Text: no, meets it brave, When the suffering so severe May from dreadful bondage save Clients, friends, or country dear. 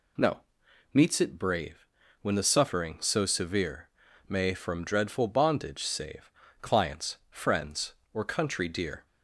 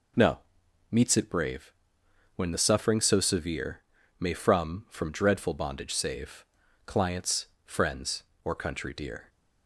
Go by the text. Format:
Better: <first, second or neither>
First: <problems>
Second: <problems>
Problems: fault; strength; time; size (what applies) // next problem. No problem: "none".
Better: first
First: pauses between "severe" and "May"; at 3.8 s; 0.38 s long // pauses between "save" and "Clients"; slight; at 6.2 s; 0.32 s long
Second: pauses between "severe" and "May"; at 3.8 s; 0.40 s long // says "from" twice; at 4.8 s // pauses between "save" and "Clients"; at 6.4 s; 0.42 s long